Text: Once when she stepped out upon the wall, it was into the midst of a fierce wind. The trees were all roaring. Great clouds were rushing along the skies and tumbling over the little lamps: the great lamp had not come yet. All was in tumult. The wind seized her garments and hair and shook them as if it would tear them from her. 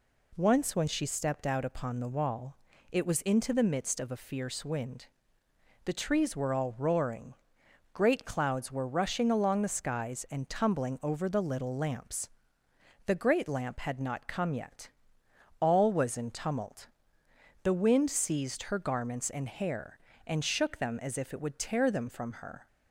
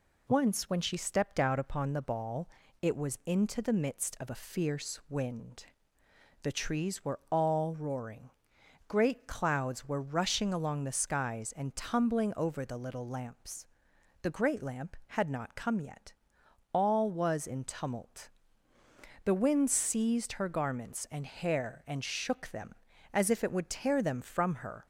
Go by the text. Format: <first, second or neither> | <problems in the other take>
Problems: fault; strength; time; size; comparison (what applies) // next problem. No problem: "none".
first | says "ball" for "wall"; at 2.0 s